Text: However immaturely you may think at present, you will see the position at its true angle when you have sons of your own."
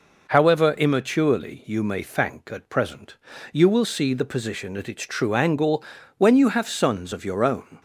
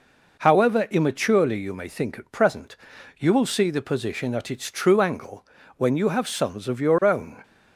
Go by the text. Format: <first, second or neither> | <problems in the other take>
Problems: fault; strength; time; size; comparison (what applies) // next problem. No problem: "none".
second | says "thank" for "think"; at 2.0 s // pauses between "angle" and "when"; slight; at 5.8 s; 0.32 s long; slight in the second